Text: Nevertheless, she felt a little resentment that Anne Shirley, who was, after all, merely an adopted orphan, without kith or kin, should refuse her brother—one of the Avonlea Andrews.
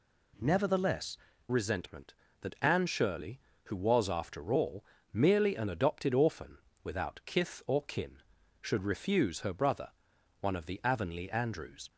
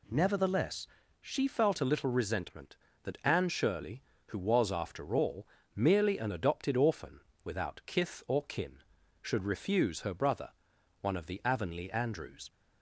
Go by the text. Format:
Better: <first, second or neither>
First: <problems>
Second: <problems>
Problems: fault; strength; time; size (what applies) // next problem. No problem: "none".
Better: second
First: skips "she felt a little"; at 1.3 s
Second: none